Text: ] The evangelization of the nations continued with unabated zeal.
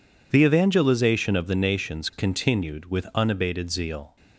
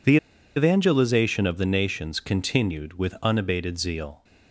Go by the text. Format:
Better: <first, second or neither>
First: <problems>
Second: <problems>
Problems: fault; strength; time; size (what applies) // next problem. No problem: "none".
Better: first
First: none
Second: pauses between "The" and "evangelization"; at 0.1 s; 0.39 s long